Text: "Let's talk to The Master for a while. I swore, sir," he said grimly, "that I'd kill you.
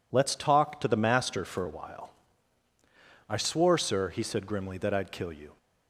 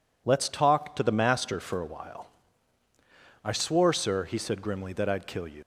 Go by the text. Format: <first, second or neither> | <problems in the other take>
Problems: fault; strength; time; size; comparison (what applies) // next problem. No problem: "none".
first | leaves "you" unfinished; at 5.6 s; 95 ms